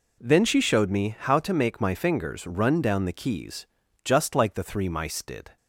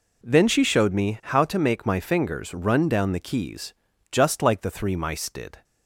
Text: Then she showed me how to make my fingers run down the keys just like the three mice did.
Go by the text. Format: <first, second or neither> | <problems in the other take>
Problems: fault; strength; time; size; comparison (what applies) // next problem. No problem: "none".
neither | pauses between "keys" and "just"; slight; the same in both